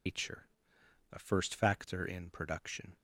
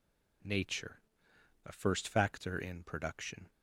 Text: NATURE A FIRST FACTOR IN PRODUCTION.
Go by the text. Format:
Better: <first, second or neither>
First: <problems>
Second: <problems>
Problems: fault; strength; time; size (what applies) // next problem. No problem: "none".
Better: second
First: loses the start of "NATURE"; at 0.0 s; 170 ms // pauses between "NATURE" and "A"; noticeable; at 0.4 s; 0.66 s long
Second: pauses between "NATURE" and "A"; noticeable; at 0.9 s; 0.66 s long